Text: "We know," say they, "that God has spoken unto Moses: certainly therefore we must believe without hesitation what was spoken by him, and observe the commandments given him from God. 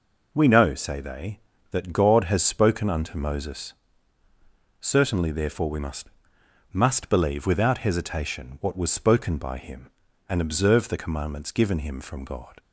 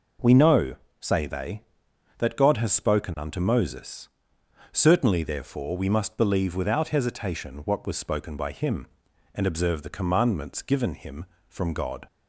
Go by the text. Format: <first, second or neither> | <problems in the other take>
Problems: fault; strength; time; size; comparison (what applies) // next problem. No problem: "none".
second | says "must" twice; at 6.7 s